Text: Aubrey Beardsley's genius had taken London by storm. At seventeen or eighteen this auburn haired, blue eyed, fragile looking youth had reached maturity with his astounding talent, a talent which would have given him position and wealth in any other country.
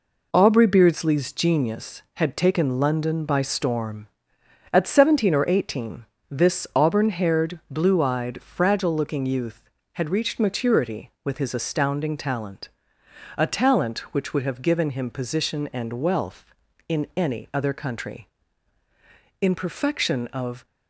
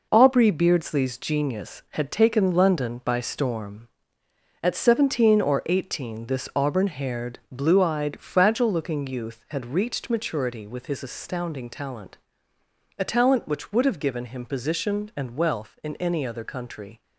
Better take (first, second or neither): second